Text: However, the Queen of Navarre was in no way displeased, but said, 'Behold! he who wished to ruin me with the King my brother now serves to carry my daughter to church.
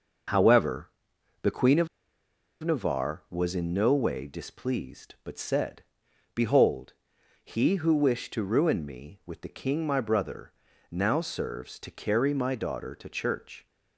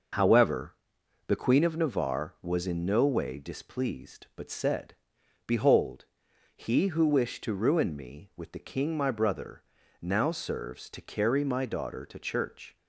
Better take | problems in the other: second | pauses between "of" and "Navarre"; noticeable; at 1.8 s; 0.76 s long // pauses between "brother" and "now"; at 10.5 s; 0.40 s long; also in the second

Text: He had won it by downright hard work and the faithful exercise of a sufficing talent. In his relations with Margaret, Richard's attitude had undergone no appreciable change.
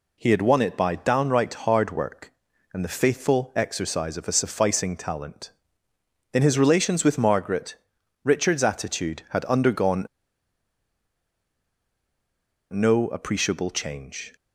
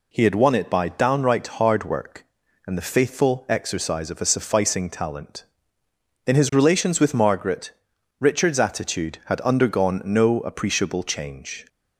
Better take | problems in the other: second | pauses between "undergone" and "no"; strong; at 10.0 s; 2.6 s long

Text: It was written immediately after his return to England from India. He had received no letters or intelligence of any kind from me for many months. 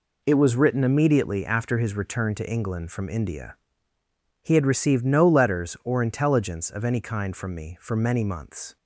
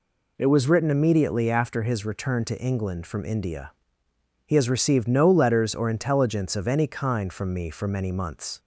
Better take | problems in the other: first | says "has" for "had"; at 4.5 s

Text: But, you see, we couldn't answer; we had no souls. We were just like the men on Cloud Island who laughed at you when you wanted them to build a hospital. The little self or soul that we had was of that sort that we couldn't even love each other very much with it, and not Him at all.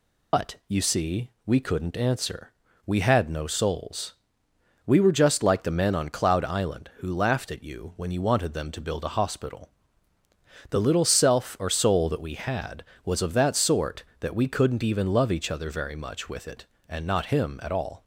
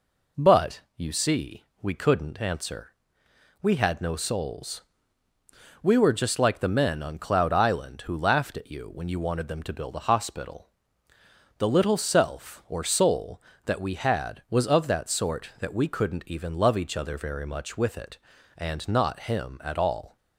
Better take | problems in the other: second | loses the start of "But"; at 0.3 s; 90 ms

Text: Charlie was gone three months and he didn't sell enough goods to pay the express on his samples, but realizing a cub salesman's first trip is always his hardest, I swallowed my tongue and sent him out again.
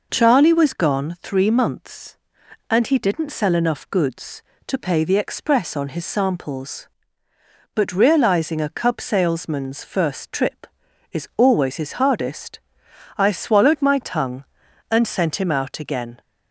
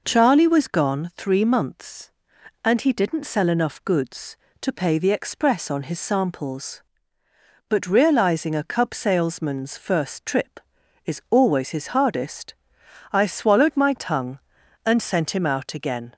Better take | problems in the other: neither | none

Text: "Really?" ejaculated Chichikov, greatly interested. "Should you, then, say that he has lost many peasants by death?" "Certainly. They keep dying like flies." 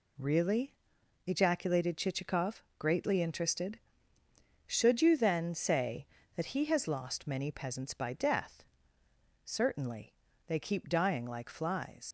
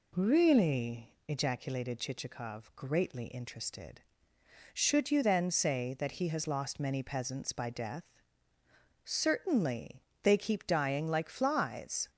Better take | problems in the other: second | leaves "flies" unfinished; at 12.0 s; 70 ms

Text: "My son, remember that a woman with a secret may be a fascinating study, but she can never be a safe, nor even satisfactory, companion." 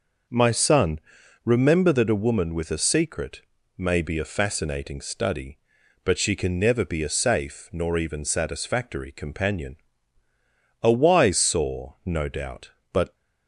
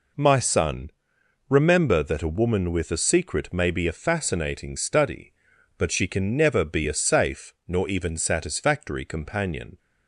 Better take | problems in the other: second | pauses between "secret" and "may"; slight; at 3.4 s; 0.36 s long // goes on to say "A wise saw no doubt but"; strong; from 10.8 s on; 2.3 s long

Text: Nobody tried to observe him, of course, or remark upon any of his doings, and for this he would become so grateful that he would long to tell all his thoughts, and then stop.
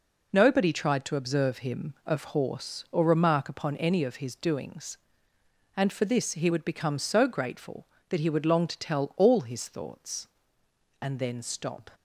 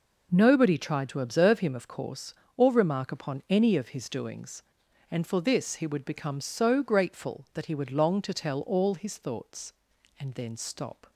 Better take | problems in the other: second | says "horse" for "course"; at 2.2 s

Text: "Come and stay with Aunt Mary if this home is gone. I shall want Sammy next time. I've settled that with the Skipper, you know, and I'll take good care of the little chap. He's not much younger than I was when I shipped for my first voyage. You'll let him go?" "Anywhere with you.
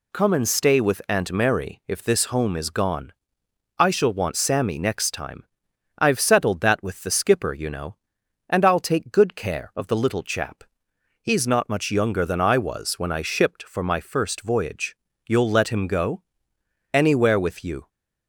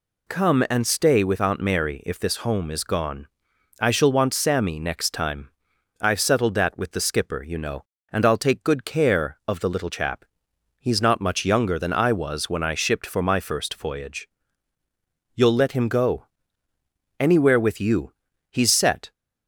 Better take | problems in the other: first | goes on to say "He's set"; from 18.5 s on; 0.60 s long

